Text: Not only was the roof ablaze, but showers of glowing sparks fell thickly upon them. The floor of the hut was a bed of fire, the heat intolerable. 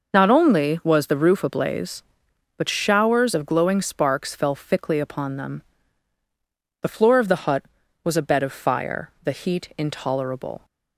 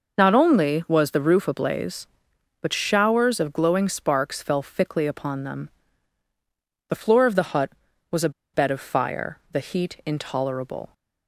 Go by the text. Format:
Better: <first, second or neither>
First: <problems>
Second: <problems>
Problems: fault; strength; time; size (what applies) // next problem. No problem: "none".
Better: first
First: none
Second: pauses between "a" and "bed"; slight; at 8.2 s; 0.23 s long